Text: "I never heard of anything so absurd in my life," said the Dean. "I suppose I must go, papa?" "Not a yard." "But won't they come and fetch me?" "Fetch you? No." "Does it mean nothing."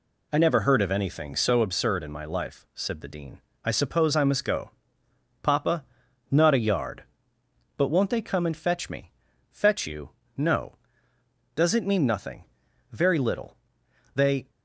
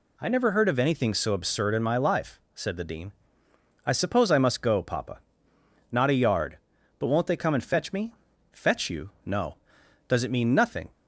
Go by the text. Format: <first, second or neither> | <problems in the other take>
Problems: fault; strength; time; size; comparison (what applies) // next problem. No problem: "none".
second | goes on to say "Very little They"; from 12.9 s on; 1.5 s long